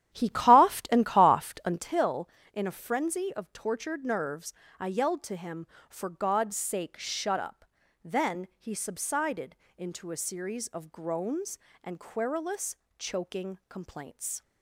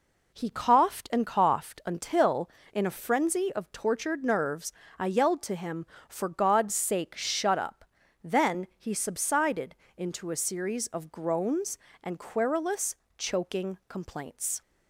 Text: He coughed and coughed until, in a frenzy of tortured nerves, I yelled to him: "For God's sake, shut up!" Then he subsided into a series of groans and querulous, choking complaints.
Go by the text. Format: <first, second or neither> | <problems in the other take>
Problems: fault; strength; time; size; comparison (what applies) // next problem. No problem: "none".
second | starts louder than the rest; strong; until 1.9 s; 11 dB // pauses between "subsided" and "into"; slight; at 9.5 s; 0.22 s long; slight in the second